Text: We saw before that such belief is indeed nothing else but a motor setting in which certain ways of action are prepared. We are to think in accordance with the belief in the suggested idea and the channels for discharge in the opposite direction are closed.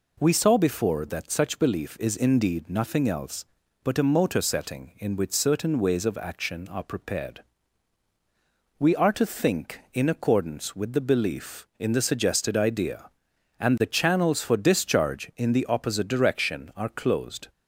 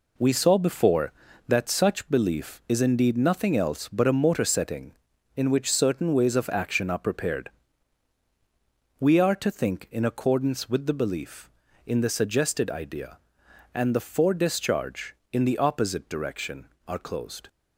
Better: first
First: none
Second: skips "channels"; at 13.9 s

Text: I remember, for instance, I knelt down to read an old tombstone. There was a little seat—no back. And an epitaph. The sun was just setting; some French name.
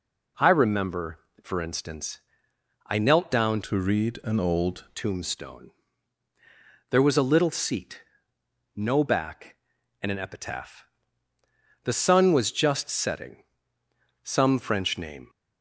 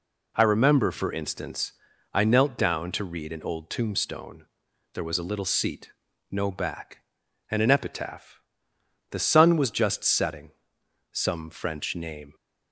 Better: second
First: changes voice from "to" to "old"; from 3.6 to 4.8 s; 1.2 s long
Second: none

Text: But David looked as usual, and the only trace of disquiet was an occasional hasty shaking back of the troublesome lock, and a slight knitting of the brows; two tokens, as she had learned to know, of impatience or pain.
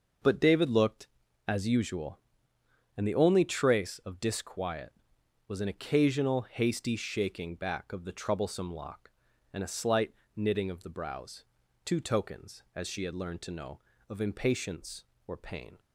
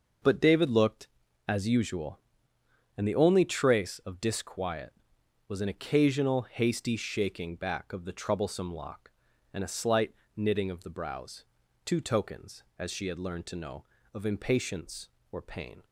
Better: neither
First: pauses between "slight" and "knitting"; slight; at 10.1 s; 0.24 s long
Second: pauses between "slight" and "knitting"; slight; at 10.1 s; 0.24 s long

